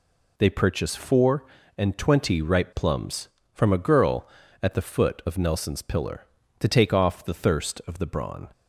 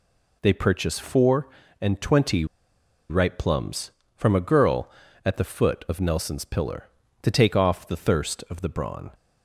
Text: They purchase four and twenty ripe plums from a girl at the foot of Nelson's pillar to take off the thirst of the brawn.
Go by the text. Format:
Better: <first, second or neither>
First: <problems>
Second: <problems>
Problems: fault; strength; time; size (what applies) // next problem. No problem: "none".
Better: first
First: none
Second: pauses between "twenty" and "ripe"; noticeable; at 2.4 s; 0.64 s long